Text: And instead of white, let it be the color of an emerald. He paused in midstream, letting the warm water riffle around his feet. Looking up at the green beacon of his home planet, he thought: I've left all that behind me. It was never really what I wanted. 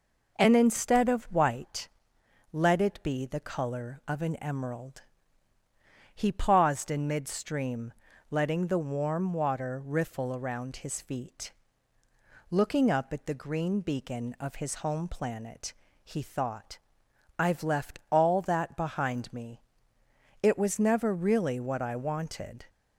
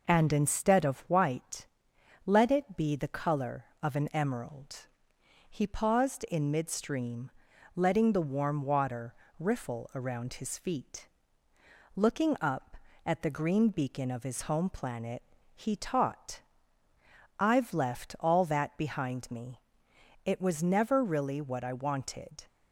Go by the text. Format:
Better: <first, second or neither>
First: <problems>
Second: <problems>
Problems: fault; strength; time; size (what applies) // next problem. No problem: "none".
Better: first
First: none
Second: pauses between "water" and "riffle"; slight; at 9.1 s; 0.24 s long // says "taught" for "thought"; at 15.7 s